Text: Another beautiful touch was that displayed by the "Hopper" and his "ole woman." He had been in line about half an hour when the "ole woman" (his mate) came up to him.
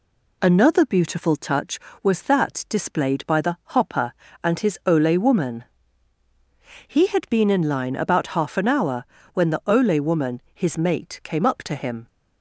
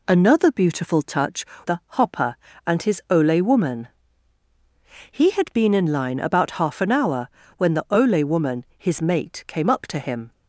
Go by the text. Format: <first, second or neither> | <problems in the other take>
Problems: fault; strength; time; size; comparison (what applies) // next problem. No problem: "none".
first | skips "was that displayed by"; at 1.5 s // pauses between "the" and "Hopper"; slight; at 1.7 s; 0.18 s long; slight in the first // pauses between "hour" and "when"; slight; at 7.2 s; 0.30 s long; slight in the first